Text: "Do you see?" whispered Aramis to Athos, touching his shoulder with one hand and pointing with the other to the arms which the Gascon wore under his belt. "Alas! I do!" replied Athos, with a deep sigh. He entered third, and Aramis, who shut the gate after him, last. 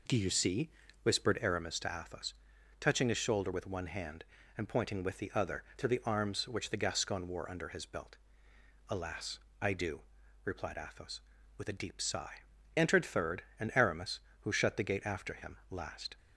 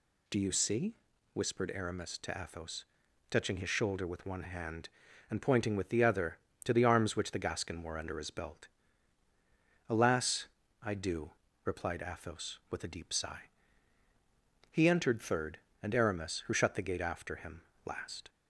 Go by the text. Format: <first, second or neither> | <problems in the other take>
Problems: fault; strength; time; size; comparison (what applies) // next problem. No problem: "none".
second | skips "He"; at 12.5 s